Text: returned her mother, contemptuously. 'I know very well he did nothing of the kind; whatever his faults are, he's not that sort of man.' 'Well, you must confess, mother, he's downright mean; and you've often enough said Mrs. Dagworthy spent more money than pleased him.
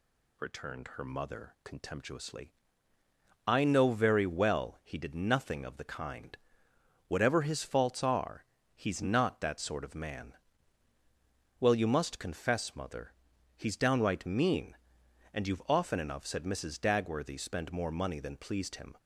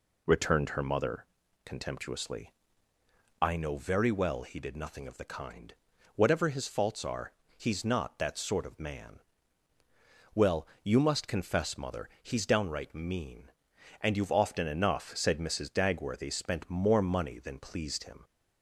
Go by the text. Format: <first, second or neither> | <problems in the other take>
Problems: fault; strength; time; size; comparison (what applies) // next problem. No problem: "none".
neither | none